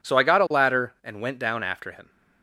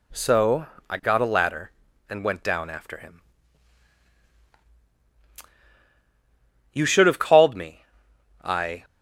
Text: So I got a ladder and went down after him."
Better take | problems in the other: first | pauses between "So" and "I"; slight; at 0.6 s; 0.24 s long // goes on to say "You should have called me I"; strong; from 6.7 s on; 2.1 s long

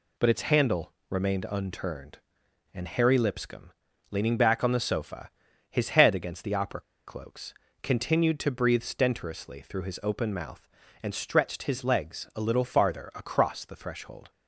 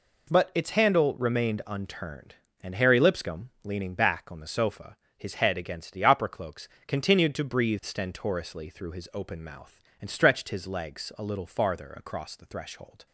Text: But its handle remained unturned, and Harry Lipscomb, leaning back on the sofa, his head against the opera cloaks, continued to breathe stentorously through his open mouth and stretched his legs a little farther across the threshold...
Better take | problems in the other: second | pauses between "handle" and "remained"; slight; at 0.9 s; 0.16 s long // pauses between "opera" and "cloaks"; slight; at 6.8 s; 0.25 s long

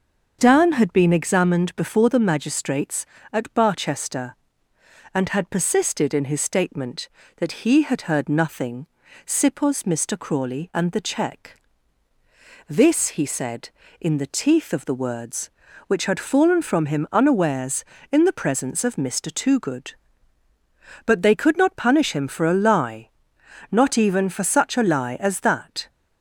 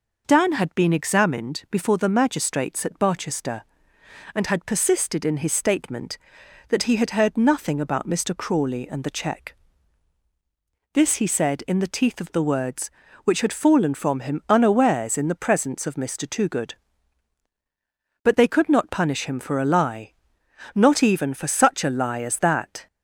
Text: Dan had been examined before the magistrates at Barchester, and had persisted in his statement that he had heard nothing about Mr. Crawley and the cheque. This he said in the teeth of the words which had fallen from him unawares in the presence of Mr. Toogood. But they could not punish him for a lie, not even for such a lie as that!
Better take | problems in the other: second | starts louder than the rest; until 1.4 s; 6.5 dB // says "sipos" for "about"; at 9.2 s

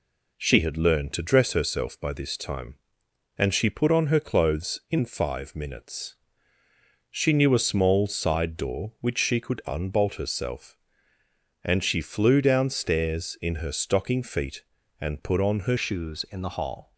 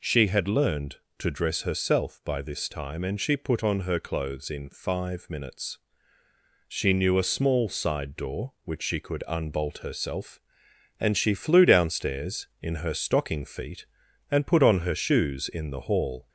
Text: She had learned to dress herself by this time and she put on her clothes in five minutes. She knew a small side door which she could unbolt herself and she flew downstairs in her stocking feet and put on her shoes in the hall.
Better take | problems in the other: second | changes voice at "shoes"; from 15.7 s on; 1.2 s long

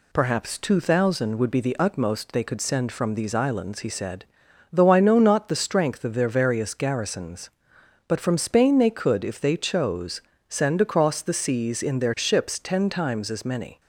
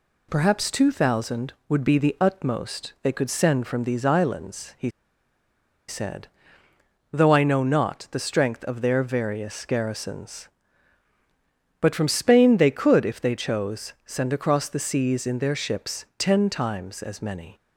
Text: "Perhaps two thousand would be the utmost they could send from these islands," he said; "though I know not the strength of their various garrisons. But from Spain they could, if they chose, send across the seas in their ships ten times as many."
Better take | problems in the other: first | pauses between "he" and "said"; at 4.8 s; 0.98 s long

